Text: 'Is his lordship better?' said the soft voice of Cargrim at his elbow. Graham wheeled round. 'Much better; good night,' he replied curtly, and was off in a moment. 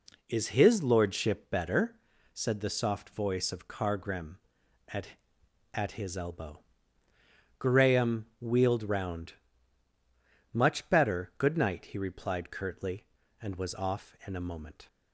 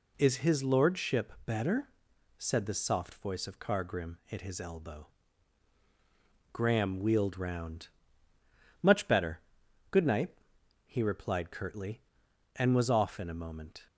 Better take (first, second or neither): second